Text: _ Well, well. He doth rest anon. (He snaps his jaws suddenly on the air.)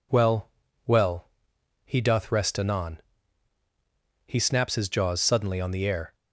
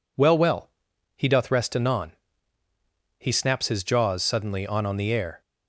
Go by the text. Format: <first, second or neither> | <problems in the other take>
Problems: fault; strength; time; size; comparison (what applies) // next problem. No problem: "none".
first | says "on" twice; at 4.8 s